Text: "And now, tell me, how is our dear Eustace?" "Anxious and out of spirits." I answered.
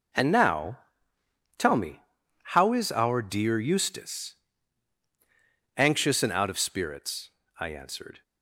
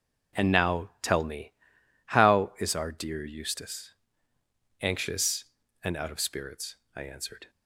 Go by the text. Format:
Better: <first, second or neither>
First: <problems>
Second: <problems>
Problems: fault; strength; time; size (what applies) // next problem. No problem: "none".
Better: neither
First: none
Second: none